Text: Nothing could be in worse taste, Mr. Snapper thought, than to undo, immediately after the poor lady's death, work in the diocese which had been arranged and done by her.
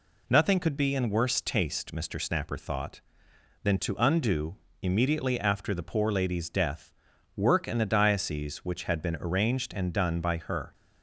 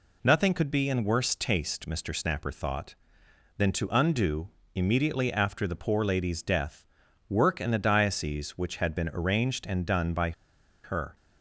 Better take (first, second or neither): first